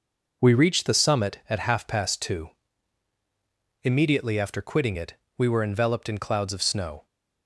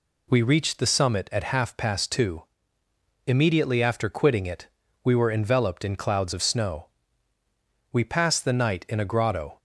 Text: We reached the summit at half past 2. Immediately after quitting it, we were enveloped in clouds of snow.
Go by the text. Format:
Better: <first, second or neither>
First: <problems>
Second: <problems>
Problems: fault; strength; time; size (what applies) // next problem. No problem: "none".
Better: first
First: none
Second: goes on to say "We passed the night in a grotto"; from 7.9 s on; 1.6 s long